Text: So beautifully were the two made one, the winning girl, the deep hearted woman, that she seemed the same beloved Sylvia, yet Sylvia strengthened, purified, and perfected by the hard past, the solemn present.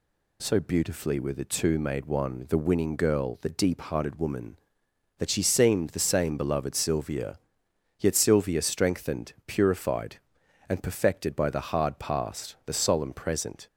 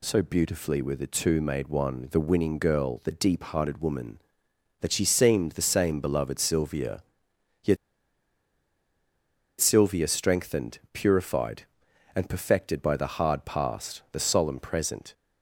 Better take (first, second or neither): first